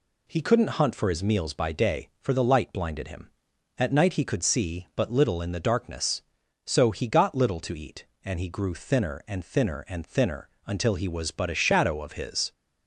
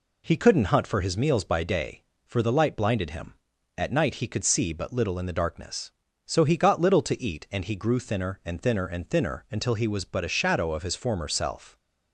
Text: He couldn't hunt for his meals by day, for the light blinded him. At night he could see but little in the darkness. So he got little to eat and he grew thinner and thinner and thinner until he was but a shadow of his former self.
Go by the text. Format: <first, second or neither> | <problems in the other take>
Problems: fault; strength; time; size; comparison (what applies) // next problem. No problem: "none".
second | pauses between "thinner" and "until"; slight; at 10.4 s; 0.16 s long // stops before "former self"; at 12.5 s